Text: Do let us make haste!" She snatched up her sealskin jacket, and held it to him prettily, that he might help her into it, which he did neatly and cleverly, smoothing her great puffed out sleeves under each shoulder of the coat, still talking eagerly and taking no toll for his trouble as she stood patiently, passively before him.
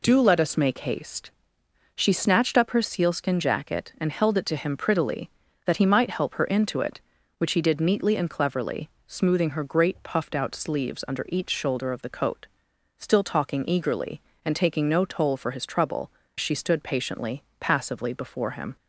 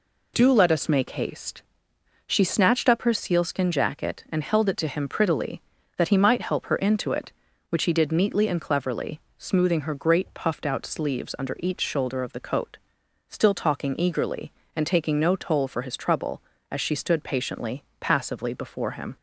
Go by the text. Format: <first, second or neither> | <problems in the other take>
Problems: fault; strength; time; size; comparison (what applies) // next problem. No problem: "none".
second | skips "as"; at 16.2 s